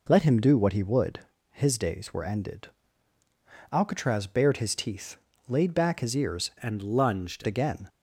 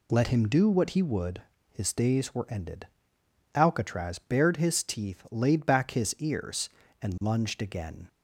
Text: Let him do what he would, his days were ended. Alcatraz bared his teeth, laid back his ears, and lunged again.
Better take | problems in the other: second | changes voice from "and" to "lunged"; from 6.5 to 7.4 s; 0.9 s long

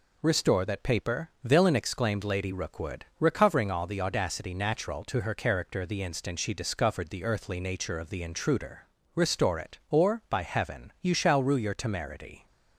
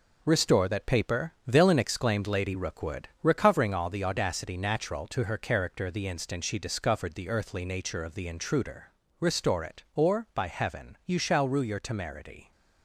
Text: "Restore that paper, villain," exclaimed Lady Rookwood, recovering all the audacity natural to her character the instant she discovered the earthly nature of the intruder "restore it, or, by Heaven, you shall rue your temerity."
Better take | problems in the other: first | gets quieter; noticeable; throughout; 6 dB // pauses between "intruder" and "restore"; slight; at 8.9 s; 0.28 s long; slight in the first

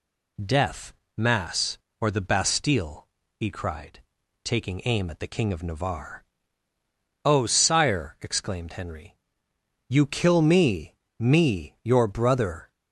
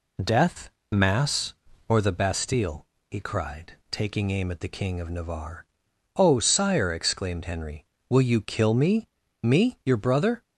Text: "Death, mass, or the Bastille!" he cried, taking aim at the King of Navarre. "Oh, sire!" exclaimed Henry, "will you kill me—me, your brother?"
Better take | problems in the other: second | skips "will"; at 9.5 s

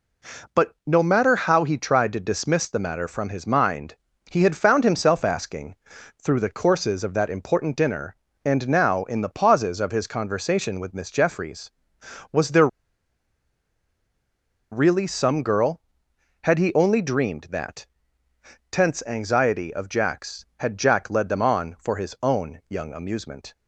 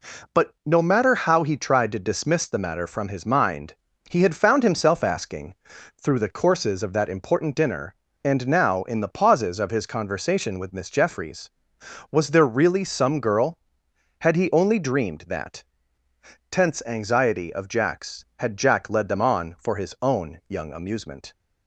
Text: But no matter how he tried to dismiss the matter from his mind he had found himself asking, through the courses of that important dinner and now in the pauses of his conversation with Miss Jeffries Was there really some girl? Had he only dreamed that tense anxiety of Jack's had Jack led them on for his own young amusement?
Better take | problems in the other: second | pauses between "mind" and "he"; slight; at 3.9 s; 0.34 s long; slight in the second // pauses between "there" and "really"; strong; at 12.6 s; 2.0 s long // pauses between "that" and "tense"; noticeable; at 17.8 s; 0.86 s long; noticeable in the second

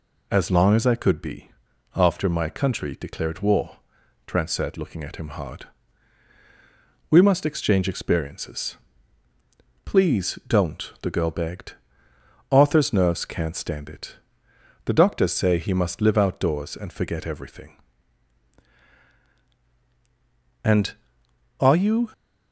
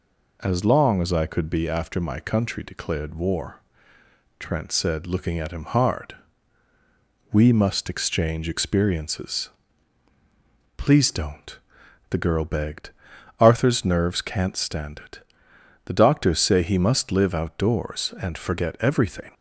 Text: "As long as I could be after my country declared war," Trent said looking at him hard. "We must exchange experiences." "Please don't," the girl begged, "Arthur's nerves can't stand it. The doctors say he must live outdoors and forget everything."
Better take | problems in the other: second | pauses between "be" and "after"; noticeable; at 1.5 s; 0.46 s long // goes on to say "And are you"; from 20.6 s on; 1.4 s long

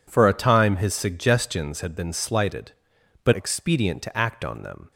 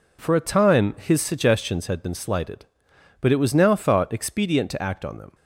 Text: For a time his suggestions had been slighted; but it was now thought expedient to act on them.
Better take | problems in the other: second | skips "it was now thought"; at 3.3 s

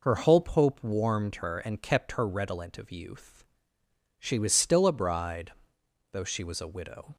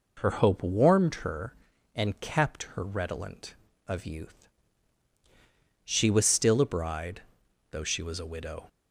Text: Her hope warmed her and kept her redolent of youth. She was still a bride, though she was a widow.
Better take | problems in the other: second | says "hope" twice; at 0.4 s

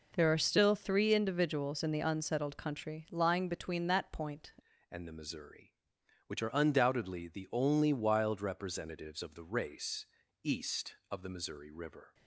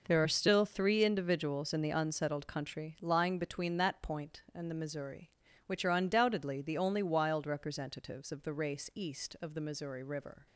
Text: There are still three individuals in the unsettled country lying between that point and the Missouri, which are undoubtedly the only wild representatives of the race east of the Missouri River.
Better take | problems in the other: second | changes voice at "and"; from 4.8 s on; 7.3 s long // pauses between "race" and "east"; at 10.0 s; 0.38 s long

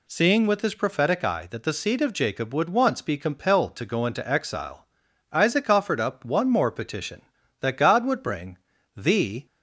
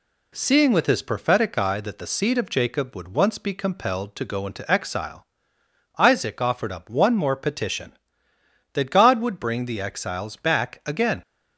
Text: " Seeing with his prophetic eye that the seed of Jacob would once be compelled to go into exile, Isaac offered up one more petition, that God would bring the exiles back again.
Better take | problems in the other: second | pauses between "bring" and "the"; at 8.5 s; 0.38 s long // stops before "exiles back again"; at 9.4 s

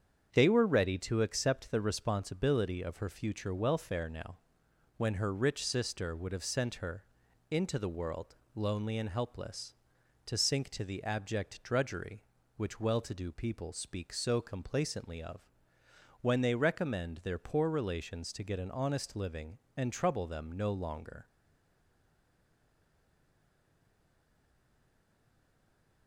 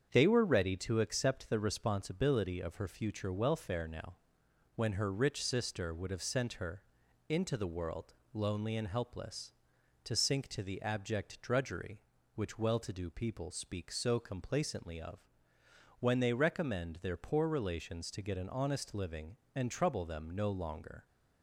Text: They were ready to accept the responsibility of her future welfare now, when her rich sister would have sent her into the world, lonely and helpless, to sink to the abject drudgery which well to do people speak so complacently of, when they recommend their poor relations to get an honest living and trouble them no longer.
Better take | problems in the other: second | starts louder than the rest; strong; until 1.3 s; 7.5 dB; strong in the second // pauses between "her" and "into"; noticeable; at 7.0 s; 0.48 s long; noticeable in the second // stays silent after the last word; strong; from 21.2 s on; 4.8 s long

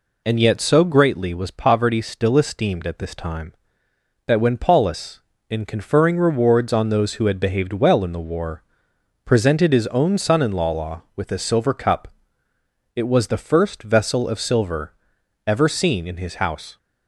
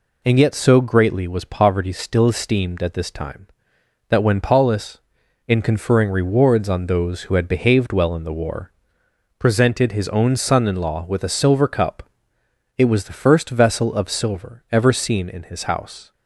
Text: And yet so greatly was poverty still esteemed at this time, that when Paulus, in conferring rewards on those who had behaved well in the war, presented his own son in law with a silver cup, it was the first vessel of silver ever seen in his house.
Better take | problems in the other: second | says "law" twice; at 10.7 s // pauses between "silver" and "ever"; noticeable; at 14.9 s; 0.54 s long

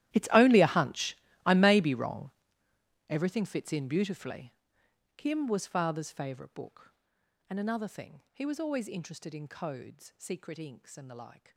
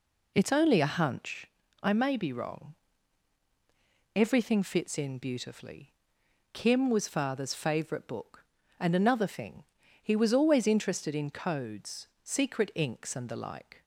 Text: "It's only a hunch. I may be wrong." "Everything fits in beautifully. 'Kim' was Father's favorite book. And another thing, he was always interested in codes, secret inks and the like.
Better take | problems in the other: second | gets quieter; strong; throughout; 20 dB

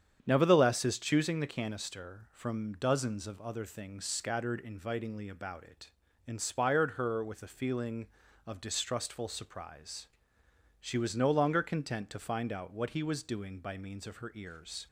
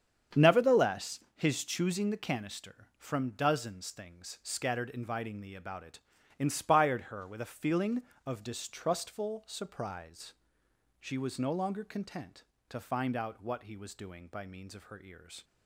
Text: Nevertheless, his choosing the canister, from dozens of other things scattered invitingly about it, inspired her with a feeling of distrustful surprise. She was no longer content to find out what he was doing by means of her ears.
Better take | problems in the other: first | starts louder than the rest; strong; until 1.5 s; 8 dB; strong in the first // skips "of other"; at 3.8 s

